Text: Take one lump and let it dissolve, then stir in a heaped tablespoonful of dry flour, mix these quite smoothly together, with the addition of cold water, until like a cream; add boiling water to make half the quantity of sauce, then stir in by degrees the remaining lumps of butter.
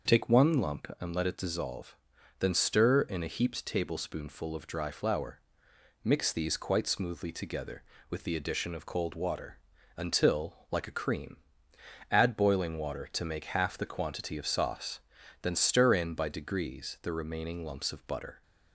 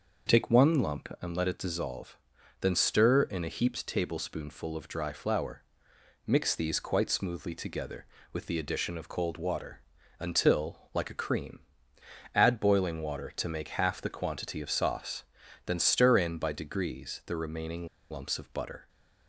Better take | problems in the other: first | starts louder than the rest; noticeable; until 1.4 s; 6 dB; noticeable in the first // pauses between "remaining" and "lumps"; slight; at 17.8 s; 0.23 s long

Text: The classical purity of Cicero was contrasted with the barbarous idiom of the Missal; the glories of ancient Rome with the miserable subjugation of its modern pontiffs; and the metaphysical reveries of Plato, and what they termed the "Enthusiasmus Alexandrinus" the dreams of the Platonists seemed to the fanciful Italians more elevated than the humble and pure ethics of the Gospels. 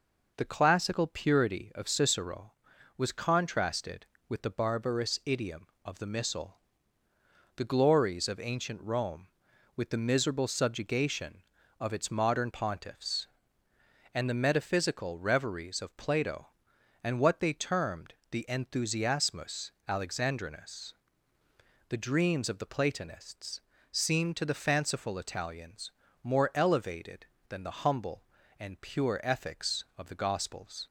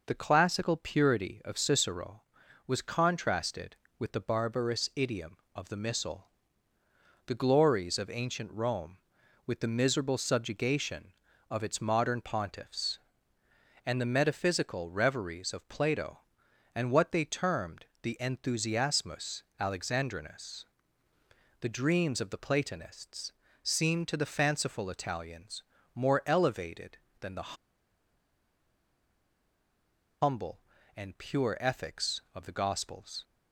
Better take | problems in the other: first | pauses between "termed" and "the"; slight; at 17.8 s; 0.16 s long; slight in the first // pauses between "Enthusiasmus" and "Alexandrinus"; slight; at 19.4 s; 0.16 s long; slight in the first // pauses between "Alexandrinus" and "the"; noticeable; at 20.6 s; 0.96 s long; noticeable in the first // pauses between "Platonists" and "seemed"; slight; at 23.3 s; 0.30 s long; slight in the first // pauses between "Italians" and "more"; slight; at 25.6 s; 0.32 s long; slight in the first // pauses between "the" and "humble"; strong; at 27.5 s; 2.6 s long

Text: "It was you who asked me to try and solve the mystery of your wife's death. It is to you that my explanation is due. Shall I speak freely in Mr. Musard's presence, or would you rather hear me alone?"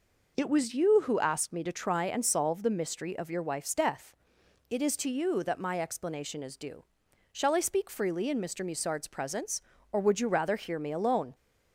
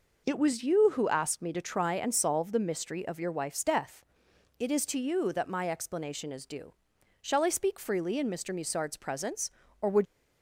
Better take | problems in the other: first | stops before "you rather hear me alone"; at 10.0 s

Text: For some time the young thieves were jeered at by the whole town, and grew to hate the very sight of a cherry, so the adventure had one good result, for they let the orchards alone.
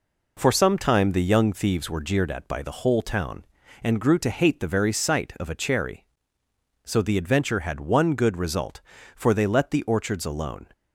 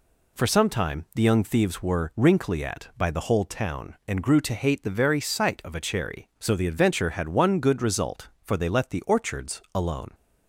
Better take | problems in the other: first | says "wrinkly" for "jeered"; at 2.1 s

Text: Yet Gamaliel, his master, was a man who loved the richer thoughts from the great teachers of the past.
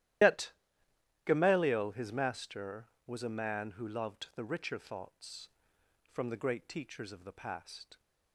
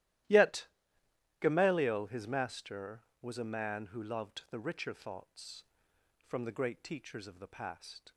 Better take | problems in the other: second | loses the start of "Yet"; at 0.2 s; 100 ms // starts louder than the rest; strong; until 1.9 s; 13.5 dB; strong in the second // pauses between "Yet" and "Gamaliel"; noticeable; at 0.5 s; 0.72 s long; noticeable in the second

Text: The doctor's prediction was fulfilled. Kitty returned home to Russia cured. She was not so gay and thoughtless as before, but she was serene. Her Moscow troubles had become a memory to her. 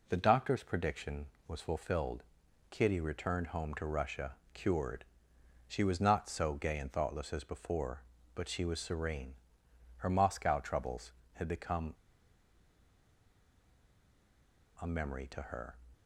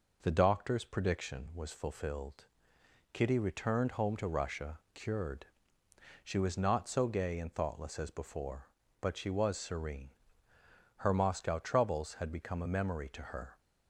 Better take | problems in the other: second | pauses between "Russia" and "cured"; slight; at 4.3 s; 0.18 s long // pauses between "become" and "a"; strong; at 11.9 s; 2.8 s long

